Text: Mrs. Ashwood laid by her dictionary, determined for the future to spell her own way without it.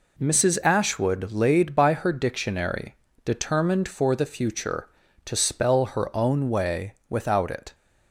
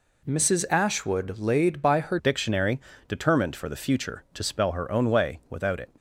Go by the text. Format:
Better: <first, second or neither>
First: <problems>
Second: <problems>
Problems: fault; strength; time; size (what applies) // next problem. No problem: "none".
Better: first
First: none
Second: changes voice at "dictionary"; from 2.1 s on; 3.8 s long